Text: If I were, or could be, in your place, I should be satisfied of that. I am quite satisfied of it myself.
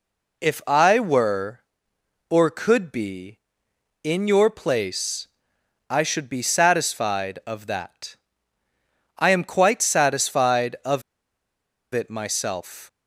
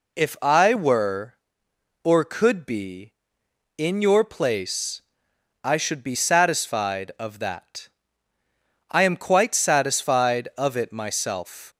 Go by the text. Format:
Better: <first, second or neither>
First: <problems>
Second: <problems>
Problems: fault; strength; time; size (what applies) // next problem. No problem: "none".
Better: second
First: pauses between "of" and "it"; noticeable; at 11.0 s; 0.90 s long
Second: none